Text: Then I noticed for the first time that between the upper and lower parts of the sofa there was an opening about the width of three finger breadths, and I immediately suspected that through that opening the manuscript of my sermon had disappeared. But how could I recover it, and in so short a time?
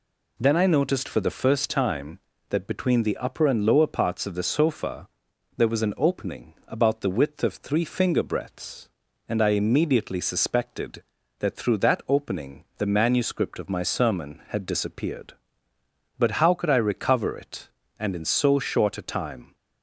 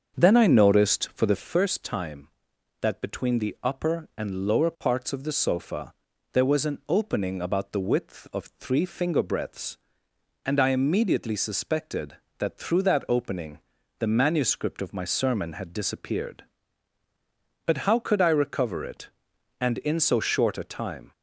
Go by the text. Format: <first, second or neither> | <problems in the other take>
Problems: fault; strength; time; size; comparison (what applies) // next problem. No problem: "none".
first | starts louder than the rest; until 1.5 s; 6.5 dB // pauses between "sofa" and "there"; at 5.9 s; 0.40 s long; noticeable in the first // pauses between "opening" and "the"; at 13.5 s; 0.40 s long